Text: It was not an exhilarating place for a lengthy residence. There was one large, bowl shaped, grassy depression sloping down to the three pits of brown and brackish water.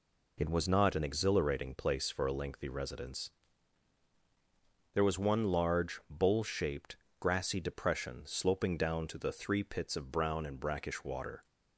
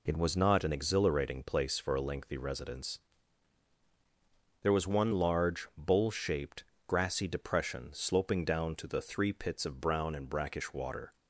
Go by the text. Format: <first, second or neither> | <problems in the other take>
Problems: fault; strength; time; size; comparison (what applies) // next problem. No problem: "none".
neither | none